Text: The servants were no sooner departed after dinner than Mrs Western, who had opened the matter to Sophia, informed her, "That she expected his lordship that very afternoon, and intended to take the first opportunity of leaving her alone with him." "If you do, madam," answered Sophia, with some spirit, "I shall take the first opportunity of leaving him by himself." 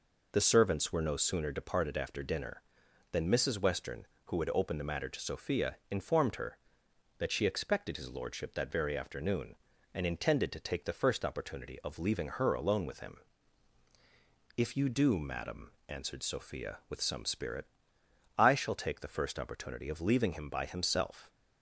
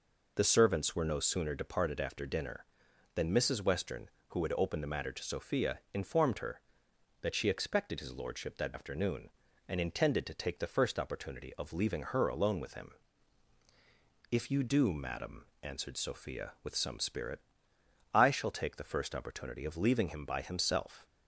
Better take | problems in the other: first | skips "very"; at 8.7 s

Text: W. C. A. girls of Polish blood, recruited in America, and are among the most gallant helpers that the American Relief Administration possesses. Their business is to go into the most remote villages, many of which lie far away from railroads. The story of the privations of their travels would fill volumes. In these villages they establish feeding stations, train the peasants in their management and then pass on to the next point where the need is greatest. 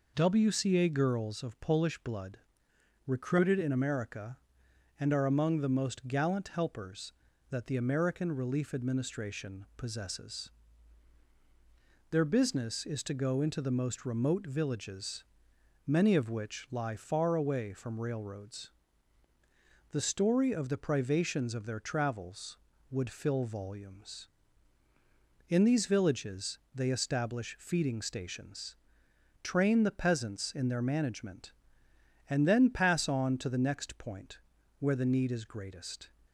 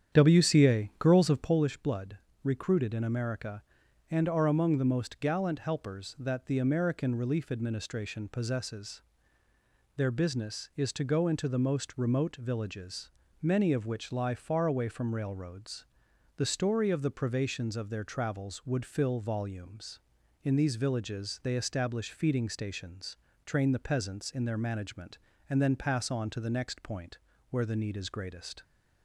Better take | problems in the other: first | starts louder than the rest; strong; until 1.7 s; 9 dB // pauses between "point" and "where"; slight; at 27.1 s; 0.34 s long; also in the first

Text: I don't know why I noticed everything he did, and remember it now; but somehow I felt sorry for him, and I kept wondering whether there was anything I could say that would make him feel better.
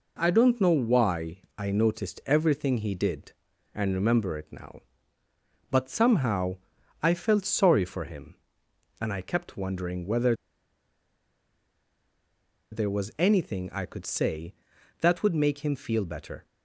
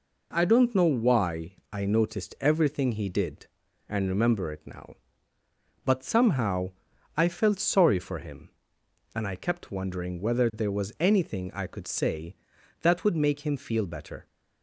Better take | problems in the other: second | pauses between "why" and "I"; slight; at 1.4 s; 0.18 s long; slight in the second // pauses between "somehow" and "I"; noticeable; at 6.5 s; 0.48 s long; noticeable in the second // pauses between "whether" and "there"; strong; at 10.3 s; 2.3 s long

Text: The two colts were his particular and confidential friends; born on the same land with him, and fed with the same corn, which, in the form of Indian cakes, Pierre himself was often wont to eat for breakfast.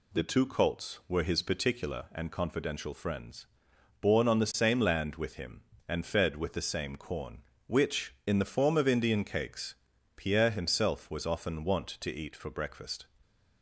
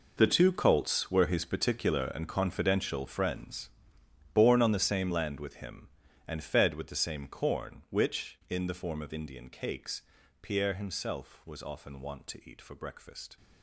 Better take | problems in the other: first | gets quieter; strong; throughout; 15 dB

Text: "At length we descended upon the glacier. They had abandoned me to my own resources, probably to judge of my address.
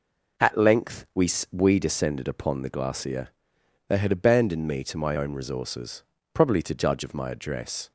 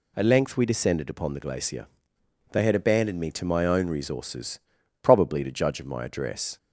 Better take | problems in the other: second | says "we" twice; at 1.5 s

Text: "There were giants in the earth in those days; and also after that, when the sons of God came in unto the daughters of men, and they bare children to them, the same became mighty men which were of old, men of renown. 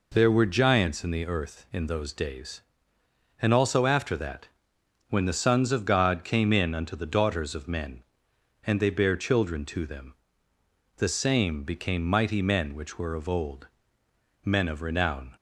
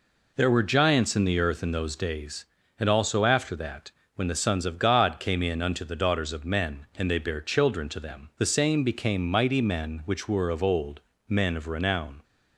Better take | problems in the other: neither | none

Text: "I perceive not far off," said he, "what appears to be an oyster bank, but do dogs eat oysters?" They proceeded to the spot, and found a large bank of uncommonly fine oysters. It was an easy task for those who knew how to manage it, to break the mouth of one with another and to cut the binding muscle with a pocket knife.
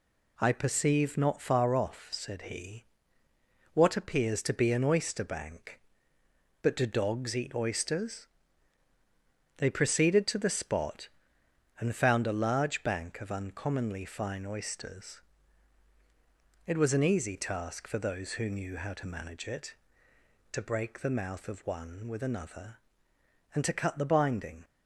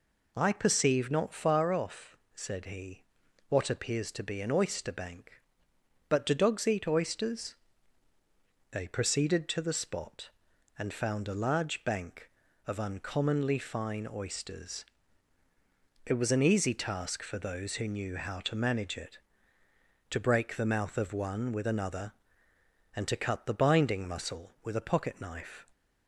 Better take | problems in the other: second | stops before "muscle with a pocket knife"; at 24.6 s

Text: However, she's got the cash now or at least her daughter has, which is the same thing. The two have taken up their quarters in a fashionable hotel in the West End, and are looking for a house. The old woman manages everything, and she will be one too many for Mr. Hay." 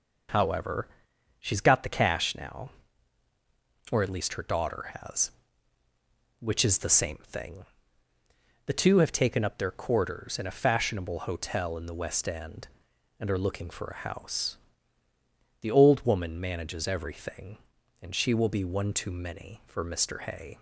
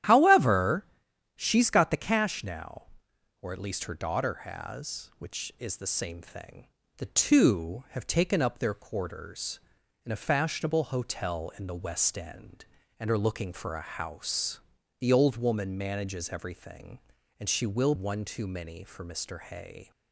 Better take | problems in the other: first | starts louder than the rest; strong; until 1.5 s; 11.5 dB // skips "be"; at 17.9 s

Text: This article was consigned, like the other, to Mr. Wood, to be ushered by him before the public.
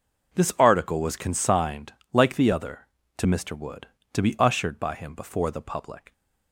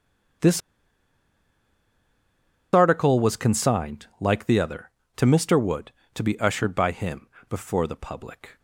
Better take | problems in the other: first | starts louder than the rest; strong; until 3.5 s; 7 dB // pauses between "This" and "article"; strong; at 0.5 s; 2.1 s long // pauses between "him" and "before"; slight; at 7.2 s; 0.24 s long

